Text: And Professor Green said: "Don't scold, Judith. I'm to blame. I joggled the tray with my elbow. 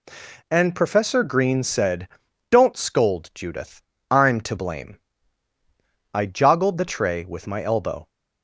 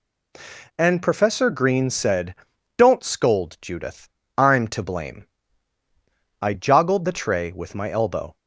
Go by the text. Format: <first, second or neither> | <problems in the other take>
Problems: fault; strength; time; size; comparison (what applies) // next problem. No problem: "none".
neither | none